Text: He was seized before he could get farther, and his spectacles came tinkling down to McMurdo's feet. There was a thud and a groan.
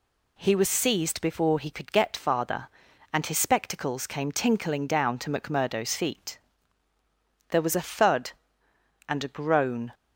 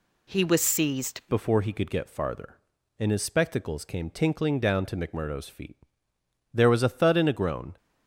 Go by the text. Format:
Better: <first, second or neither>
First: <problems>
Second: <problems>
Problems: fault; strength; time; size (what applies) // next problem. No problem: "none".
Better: first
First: none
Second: changes voice at "before"; from 1.3 s on; 6.4 s long